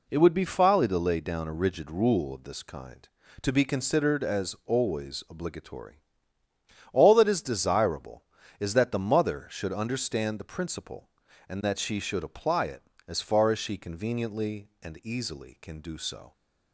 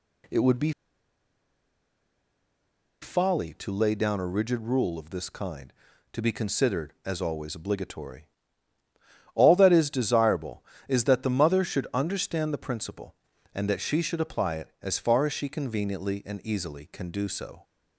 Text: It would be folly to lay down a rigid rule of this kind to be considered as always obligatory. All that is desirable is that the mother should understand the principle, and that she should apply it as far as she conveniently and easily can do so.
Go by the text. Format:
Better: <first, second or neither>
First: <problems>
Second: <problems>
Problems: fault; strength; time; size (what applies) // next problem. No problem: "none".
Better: first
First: none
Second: pauses between "be" and "folly"; strong; at 0.7 s; 2.3 s long